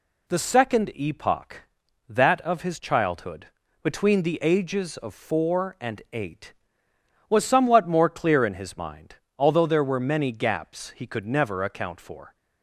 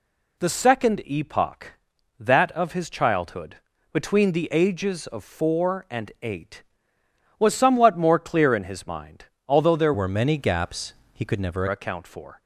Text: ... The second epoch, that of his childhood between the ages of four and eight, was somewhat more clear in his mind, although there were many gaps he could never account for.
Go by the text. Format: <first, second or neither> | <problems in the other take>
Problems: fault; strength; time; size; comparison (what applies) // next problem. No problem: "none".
first | pauses between "childhood" and "between"; slight; at 3.5 s; 0.36 s long; slight in the first // changes voice from "were" to "never"; from 9.9 to 11.6 s; 1.7 s long // pauses between "gaps" and "he"; slight; at 10.9 s; 0.20 s long